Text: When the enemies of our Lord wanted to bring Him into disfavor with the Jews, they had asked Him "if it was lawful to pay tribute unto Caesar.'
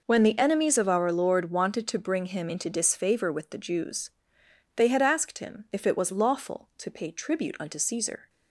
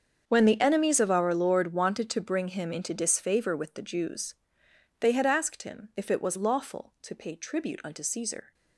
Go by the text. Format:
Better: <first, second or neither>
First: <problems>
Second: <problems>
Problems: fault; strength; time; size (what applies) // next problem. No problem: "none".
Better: first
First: none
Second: gets quieter; strong; throughout; 16 dB